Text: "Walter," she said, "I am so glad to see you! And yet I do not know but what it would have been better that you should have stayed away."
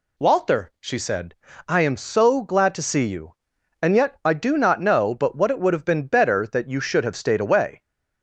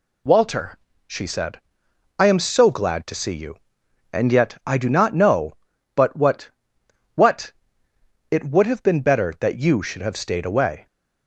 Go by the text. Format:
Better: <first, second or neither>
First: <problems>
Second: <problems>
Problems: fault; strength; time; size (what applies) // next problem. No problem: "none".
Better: first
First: none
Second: says "what" twice; at 7.1 s